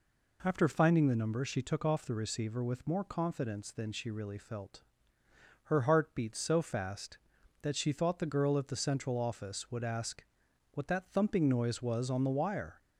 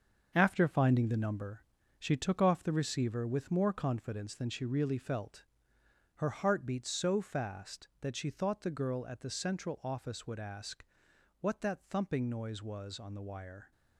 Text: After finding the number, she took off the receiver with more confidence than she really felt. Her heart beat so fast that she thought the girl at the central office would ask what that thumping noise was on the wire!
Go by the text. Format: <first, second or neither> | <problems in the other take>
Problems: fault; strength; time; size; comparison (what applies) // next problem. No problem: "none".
first | gets quieter; strong; throughout; 8 dB // pauses between "ask" and "what"; noticeable; at 10.8 s; 0.56 s long; noticeable in the first